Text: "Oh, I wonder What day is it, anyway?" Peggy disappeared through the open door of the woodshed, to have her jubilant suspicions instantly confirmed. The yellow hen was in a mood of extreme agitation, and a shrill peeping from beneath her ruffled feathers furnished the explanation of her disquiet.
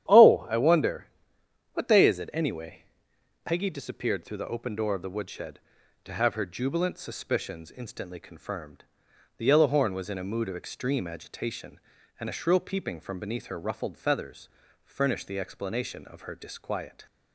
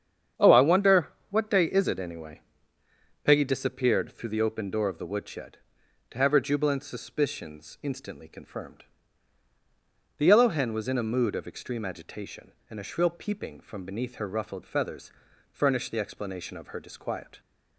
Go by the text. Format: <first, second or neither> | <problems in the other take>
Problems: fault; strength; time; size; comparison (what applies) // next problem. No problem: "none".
second | starts louder than the rest; strong; until 1.7 s; 10.5 dB; strong in the second // pauses between "wonder" and "What"; noticeable; at 1.0 s; 0.66 s long; slight in the second // says "horn" for "hen"; at 9.6 s // pauses between "feathers" and "furnished"; slight; at 14.4 s; 0.36 s long; also in the second